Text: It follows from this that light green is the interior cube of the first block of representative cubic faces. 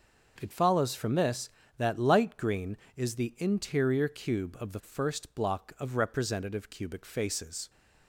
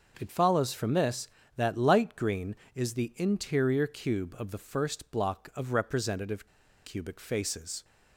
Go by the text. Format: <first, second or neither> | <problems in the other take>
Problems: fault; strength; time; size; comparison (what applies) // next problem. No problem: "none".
first | starts louder than the rest; until 1.2 s; 6.5 dB; also in the first // pauses between "representative" and "cubic"; at 6.4 s; 0.39 s long